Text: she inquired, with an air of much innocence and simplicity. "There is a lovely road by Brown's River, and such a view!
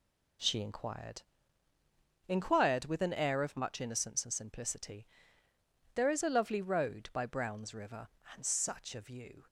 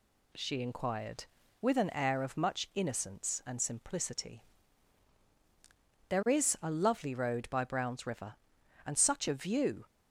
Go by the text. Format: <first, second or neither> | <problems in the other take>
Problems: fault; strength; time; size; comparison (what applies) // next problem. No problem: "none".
second | says "inquired" twice; at 2.2 s